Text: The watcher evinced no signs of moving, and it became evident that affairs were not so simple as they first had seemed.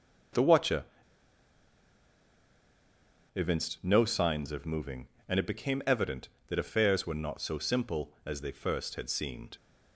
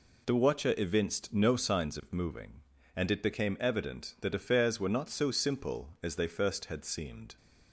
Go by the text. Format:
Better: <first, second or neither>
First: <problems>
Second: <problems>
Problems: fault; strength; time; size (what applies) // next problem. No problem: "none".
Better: second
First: pauses between "watcher" and "evinced"; strong; at 0.8 s; 2.5 s long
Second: none